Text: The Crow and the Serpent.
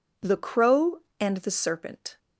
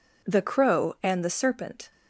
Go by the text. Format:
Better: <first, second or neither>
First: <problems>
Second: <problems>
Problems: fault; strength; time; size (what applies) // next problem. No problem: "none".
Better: neither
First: none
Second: none